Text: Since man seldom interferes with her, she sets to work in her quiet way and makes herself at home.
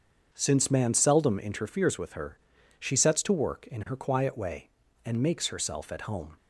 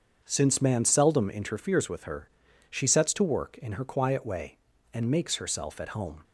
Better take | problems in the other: neither | starts louder than the rest; the same in both

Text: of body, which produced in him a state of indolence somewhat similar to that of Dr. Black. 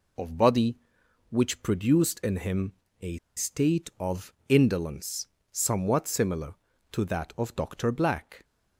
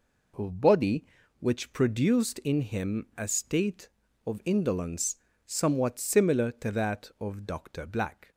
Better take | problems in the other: second | pauses between "him" and "a"; slight; at 2.7 s; 0.28 s long // pauses between "a" and "state"; slight; at 3.1 s; 0.18 s long // pauses between "of" and "indolence"; slight; at 4.3 s; 0.16 s long // pauses between "indolence" and "somewhat"; slight; at 5.2 s; 0.26 s long; slight in the second

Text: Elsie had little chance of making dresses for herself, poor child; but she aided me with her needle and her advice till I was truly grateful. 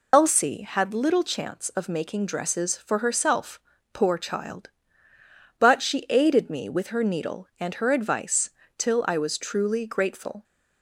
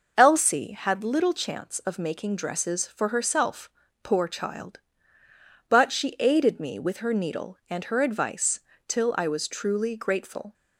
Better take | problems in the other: second | loses the start of "Elsie"; at 0.1 s; 60 ms // pauses between "advice" and "till"; slight; at 8.4 s; 0.30 s long; slight in the second

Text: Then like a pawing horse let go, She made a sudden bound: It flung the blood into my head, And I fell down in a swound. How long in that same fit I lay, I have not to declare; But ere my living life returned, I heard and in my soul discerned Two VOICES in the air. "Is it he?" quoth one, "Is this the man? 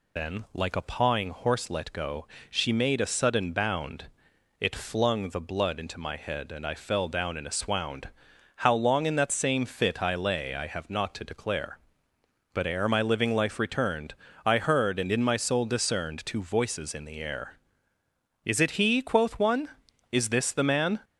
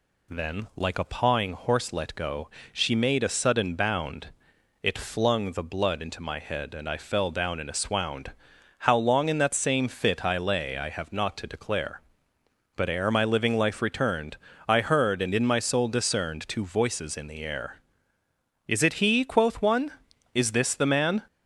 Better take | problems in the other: second | loses the start of "Then"; at 0.1 s; 90 ms

